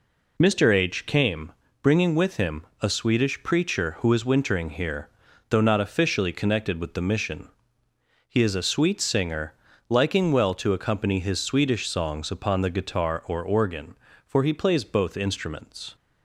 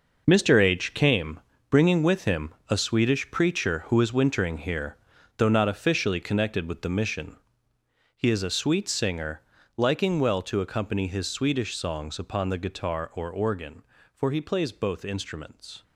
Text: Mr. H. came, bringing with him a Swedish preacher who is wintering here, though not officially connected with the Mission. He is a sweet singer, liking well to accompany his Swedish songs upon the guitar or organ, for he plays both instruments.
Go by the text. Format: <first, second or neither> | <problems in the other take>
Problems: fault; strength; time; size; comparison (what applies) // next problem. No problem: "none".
first | gets quieter; strong; throughout; 11 dB // pauses between "him" and "a"; slight; at 2.5 s; 0.18 s long; slight in the first